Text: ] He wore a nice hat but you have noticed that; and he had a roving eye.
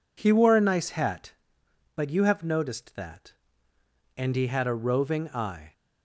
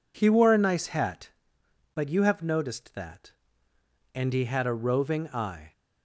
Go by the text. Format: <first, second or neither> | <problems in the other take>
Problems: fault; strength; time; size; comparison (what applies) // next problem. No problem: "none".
neither | none